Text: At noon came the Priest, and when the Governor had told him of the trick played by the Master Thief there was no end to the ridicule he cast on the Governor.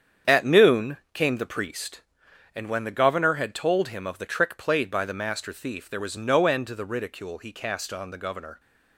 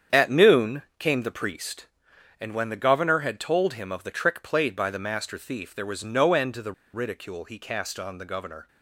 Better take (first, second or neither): first